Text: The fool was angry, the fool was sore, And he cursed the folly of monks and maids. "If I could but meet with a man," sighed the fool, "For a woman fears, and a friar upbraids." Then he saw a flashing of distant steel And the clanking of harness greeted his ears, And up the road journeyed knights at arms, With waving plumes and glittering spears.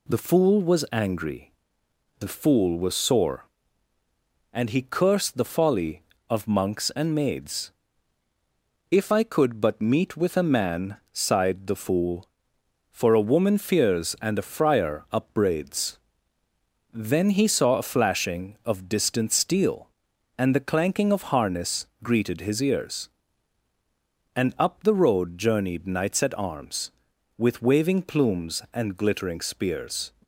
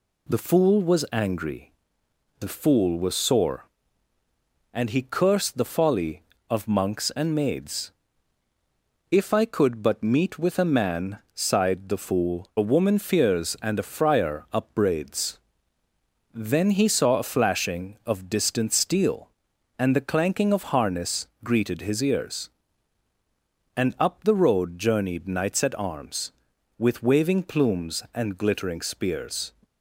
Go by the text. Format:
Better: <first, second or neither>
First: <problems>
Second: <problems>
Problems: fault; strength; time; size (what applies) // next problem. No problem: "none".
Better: first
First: pauses between "harness" and "greeted"; slight; at 21.8 s; 0.16 s long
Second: skips "For"; at 12.5 s // pauses between "harness" and "greeted"; slight; at 21.2 s; 0.16 s long